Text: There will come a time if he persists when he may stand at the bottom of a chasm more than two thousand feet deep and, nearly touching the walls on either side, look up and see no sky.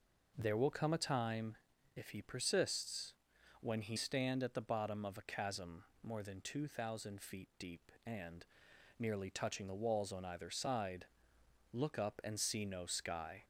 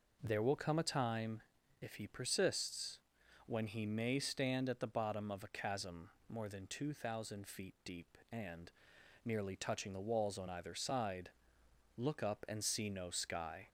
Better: second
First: pauses between "time" and "if"; at 1.5 s; 0.40 s long // pauses between "persists" and "when"; noticeable; at 3.1 s; 0.46 s long // skips "may"; at 3.9 s // pauses between "chasm" and "more"; slight; at 5.8 s; 0.18 s long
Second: pauses between "time" and "if"; at 1.4 s; 0.40 s long // pauses between "persists" and "when"; noticeable; at 2.9 s; 0.46 s long // pauses between "chasm" and "more"; slight; at 6.0 s; 0.18 s long

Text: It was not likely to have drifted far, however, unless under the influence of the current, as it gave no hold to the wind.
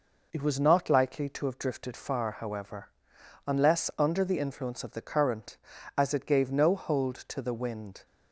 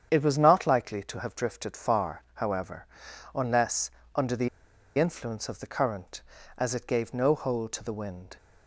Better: first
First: none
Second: starts louder than the rest; strong; until 1.1 s; 8.5 dB // pauses between "unless" and "under"; slight; at 3.8 s; 0.24 s long // pauses between "the" and "influence"; noticeable; at 4.4 s; 0.50 s long

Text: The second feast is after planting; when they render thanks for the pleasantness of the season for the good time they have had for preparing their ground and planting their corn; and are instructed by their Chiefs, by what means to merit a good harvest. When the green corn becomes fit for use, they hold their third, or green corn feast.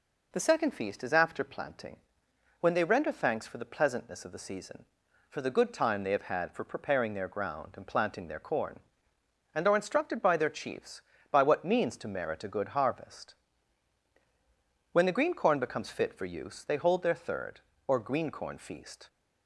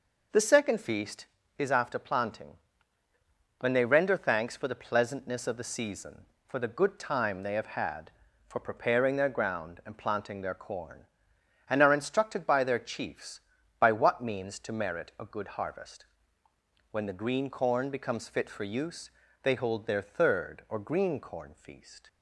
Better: neither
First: none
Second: none

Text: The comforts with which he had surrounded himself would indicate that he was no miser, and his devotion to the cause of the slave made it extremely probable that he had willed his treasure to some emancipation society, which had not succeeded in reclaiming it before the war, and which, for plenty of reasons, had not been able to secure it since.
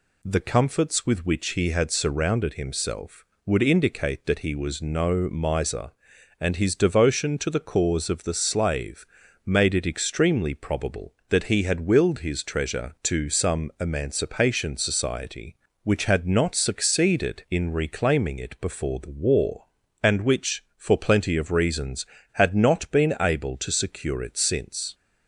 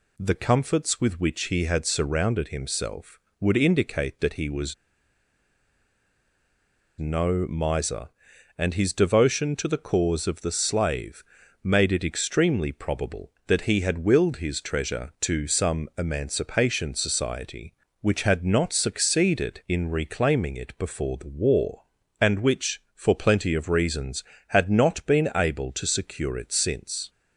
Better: first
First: pauses between "slave" and "made"; at 9.0 s; 0.40 s long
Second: pauses between "was" and "no"; strong; at 4.7 s; 2.2 s long // pauses between "slave" and "made"; at 11.2 s; 0.40 s long

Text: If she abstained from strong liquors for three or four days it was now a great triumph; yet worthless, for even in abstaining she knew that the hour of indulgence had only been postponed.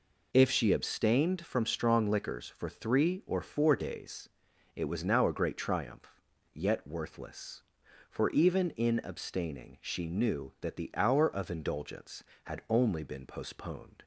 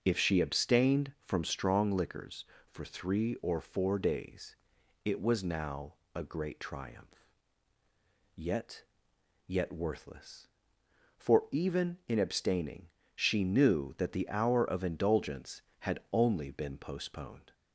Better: first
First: pauses between "days" and "it"; noticeable; at 4.2 s; 0.46 s long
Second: starts louder than the rest; noticeable; until 1.0 s; 6 dB // pauses between "days" and "it"; noticeable; at 4.5 s; 0.50 s long // pauses between "now" and "a"; slight; at 5.9 s; 0.22 s long // says "yet" twice; at 9.4 s // pauses between "abstaining" and "she"; slight; at 12.8 s; 0.26 s long

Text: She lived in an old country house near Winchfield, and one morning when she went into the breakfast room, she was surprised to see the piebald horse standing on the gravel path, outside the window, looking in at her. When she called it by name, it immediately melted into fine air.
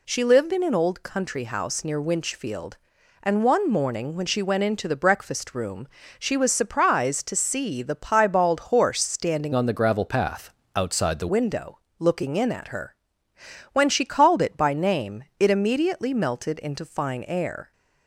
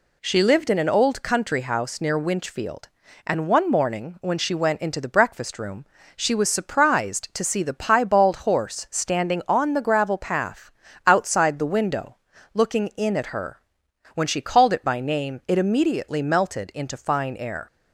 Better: second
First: changes voice from "on" to "the"; from 9.5 to 11.2 s; 1.7 s long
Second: none

